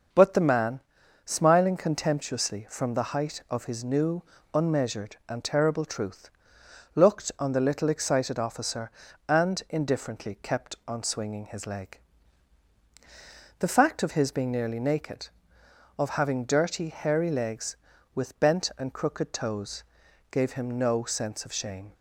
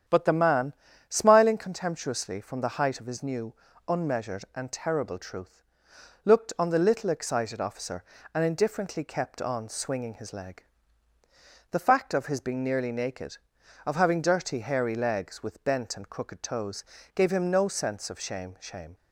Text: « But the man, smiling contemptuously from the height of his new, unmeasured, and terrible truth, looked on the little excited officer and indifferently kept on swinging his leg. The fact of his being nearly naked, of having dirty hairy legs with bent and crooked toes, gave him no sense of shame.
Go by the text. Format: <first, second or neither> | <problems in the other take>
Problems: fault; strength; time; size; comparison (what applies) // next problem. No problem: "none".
first | starts louder than the rest; strong; until 1.4 s; 9 dB; noticeable in the first // says "shame" twice; at 18.6 s